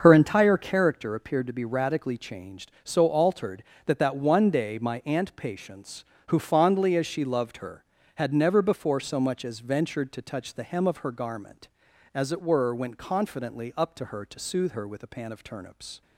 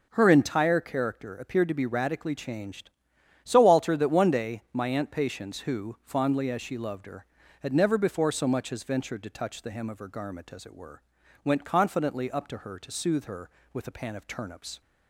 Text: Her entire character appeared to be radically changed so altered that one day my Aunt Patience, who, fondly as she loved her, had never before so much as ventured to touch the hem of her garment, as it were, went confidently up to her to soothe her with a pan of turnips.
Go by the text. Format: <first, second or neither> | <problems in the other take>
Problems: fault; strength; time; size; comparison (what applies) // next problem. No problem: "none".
second | starts louder than the rest; until 1.0 s; 6.5 dB // says "that" twice; at 3.9 s